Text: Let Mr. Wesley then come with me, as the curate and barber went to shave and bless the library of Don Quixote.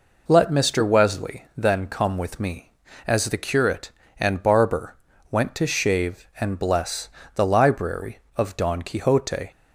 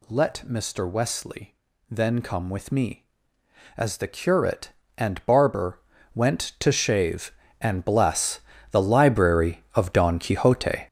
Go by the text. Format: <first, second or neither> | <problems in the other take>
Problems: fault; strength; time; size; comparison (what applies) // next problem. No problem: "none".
first | gets louder; strong; throughout; 9 dB // pauses between "Wesley" and "then"; slight; at 1.5 s; 0.34 s long // pauses between "barber" and "went"; slight; at 5.7 s; 0.34 s long; slight in the first // pauses between "bless" and "the"; slight; at 8.4 s; 0.30 s long; slight in the first